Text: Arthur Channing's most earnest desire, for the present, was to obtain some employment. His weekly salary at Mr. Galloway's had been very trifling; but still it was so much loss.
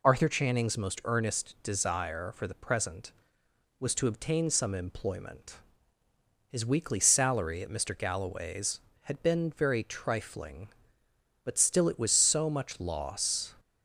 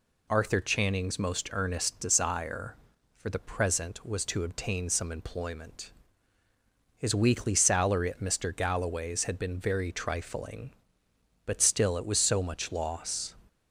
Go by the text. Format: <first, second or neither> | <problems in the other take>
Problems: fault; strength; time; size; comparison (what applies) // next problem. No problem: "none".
neither | none